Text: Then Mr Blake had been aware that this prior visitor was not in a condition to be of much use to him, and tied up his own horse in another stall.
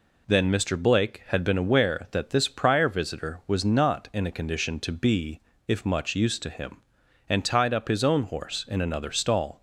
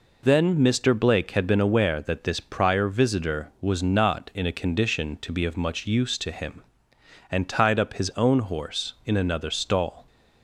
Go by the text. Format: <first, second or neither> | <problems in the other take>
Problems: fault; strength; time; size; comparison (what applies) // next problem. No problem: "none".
second | says "if" for "of"; at 5.6 s